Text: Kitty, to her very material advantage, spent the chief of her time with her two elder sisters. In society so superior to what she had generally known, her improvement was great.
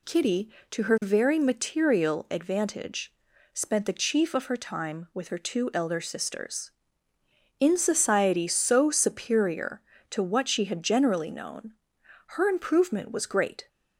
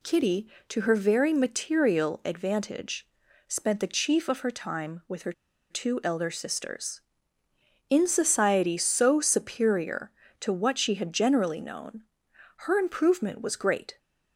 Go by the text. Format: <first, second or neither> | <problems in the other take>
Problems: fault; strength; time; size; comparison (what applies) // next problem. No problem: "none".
first | pauses between "her" and "two"; at 5.3 s; 0.38 s long